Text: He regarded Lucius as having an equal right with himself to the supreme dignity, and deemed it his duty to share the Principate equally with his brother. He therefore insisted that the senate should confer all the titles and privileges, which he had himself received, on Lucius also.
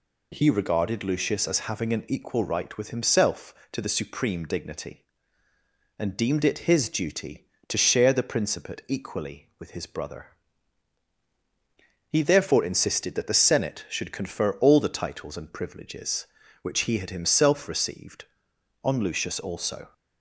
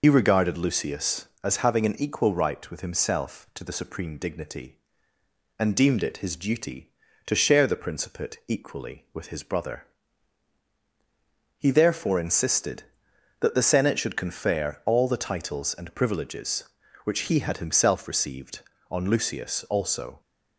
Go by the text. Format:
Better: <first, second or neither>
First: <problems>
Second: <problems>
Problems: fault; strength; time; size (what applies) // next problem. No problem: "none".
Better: first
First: none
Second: loses the start of "He"; at 0.0 s; 60 ms